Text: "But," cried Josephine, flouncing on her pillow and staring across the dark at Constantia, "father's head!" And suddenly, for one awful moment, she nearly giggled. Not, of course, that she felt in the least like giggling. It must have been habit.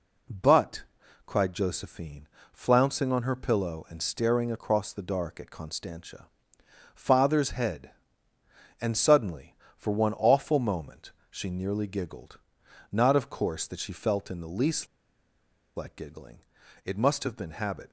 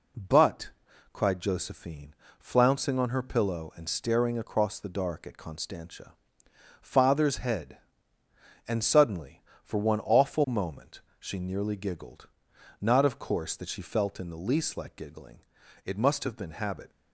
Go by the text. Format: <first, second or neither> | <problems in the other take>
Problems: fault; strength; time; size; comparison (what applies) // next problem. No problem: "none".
second | pauses between "least" and "like"; noticeable; at 14.8 s; 0.89 s long